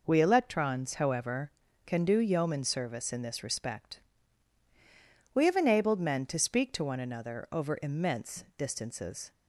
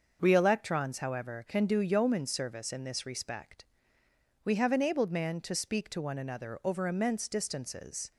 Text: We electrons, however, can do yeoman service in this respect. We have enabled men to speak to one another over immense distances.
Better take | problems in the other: first | starts louder than the rest; until 1.2 s; 6.5 dB // says "man" for "men"; at 5.1 s

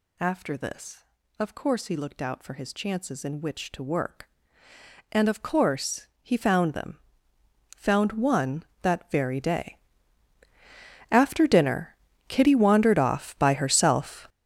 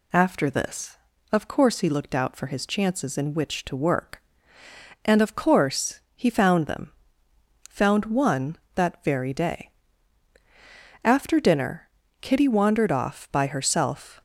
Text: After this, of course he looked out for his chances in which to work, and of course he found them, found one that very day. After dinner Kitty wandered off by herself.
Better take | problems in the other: second | gets louder; strong; throughout; 12.5 dB // pauses between "course" and "he"; slight; at 6.0 s; 0.16 s long; slight in the second // pauses between "dinner" and "Kitty"; slight; at 11.9 s; 0.34 s long; slight in the second

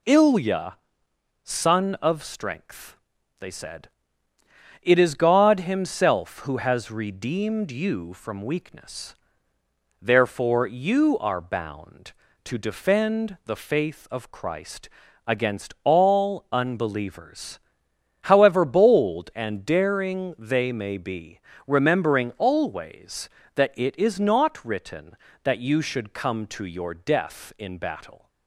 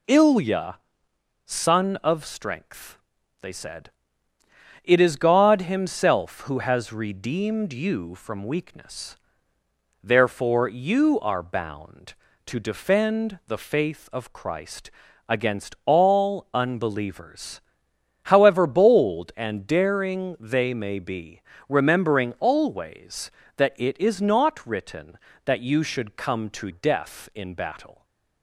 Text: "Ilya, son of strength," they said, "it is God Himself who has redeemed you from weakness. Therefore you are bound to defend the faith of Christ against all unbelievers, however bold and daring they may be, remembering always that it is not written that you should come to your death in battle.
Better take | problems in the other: first | pauses between "Christ" and "against"; slight; at 14.9 s; 0.36 s long; slight in the first // skips "your"; at 26.6 s

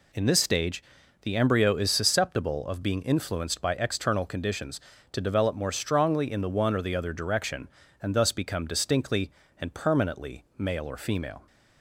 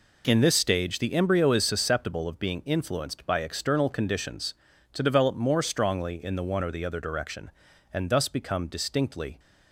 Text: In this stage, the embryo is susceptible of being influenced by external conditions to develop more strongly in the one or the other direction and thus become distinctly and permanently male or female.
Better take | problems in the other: first | stops before "and permanently male or female"; at 9.3 s

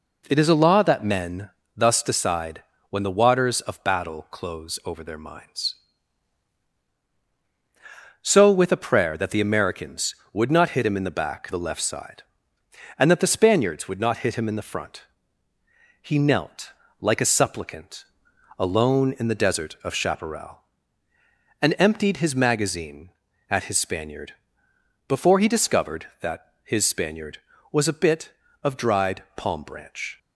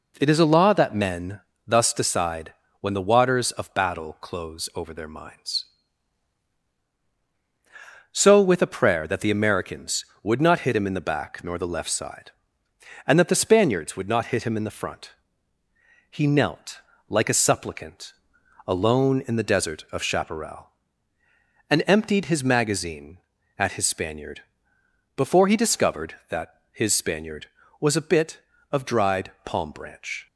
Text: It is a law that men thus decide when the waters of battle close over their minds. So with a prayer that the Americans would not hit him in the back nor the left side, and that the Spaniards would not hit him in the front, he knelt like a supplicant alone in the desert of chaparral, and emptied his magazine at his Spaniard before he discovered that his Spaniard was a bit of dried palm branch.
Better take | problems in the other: second | pauses between "men" and "thus"; slight; at 1.5 s; 0.26 s long; slight in the second // pauses between "decide" and "when"; slight; at 2.6 s; 0.26 s long; slight in the second // skips "nor"; at 11.5 s // pauses between "knelt" and "like"; slight; at 16.7 s; 0.30 s long; slight in the second // pauses between "supplicant" and "alone"; noticeable; at 18.0 s; 0.56 s long; noticeable in the second // pauses between "Spaniard" and "before"; noticeable; at 24.3 s; 0.74 s long; noticeable in the second

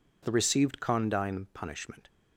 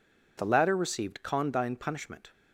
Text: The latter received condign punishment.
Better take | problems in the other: second | skips "latter"; at 0.3 s

